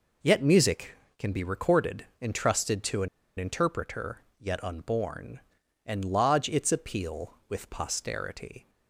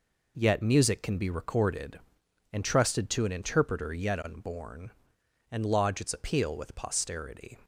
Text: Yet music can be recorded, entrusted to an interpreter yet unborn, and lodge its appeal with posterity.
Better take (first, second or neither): second